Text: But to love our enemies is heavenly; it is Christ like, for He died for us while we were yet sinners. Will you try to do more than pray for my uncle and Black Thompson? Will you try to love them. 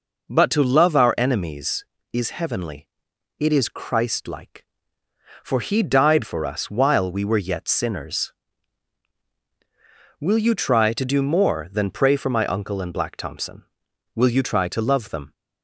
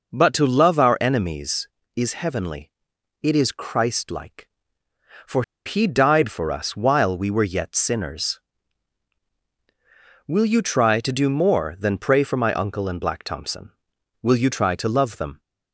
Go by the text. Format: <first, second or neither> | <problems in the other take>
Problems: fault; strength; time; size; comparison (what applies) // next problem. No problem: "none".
first | pauses between "for" and "He"; slight; at 5.4 s; 0.23 s long